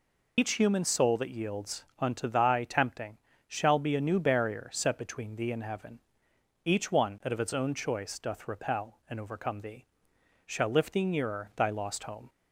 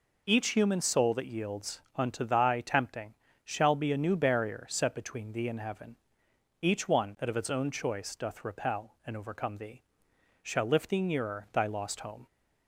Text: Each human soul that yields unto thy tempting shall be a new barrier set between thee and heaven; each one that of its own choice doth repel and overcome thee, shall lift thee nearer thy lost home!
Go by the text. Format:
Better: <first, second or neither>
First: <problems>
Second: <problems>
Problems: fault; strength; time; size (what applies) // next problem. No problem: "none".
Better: second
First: loses the start of "Each"; at 0.3 s; 90 ms // pauses between "yields" and "unto"; slight; at 1.8 s; 0.16 s long // pauses between "tempting" and "shall"; slight; at 3.1 s; 0.30 s long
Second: pauses between "yields" and "unto"; slight; at 1.7 s; 0.16 s long // pauses between "tempting" and "shall"; slight; at 3.1 s; 0.30 s long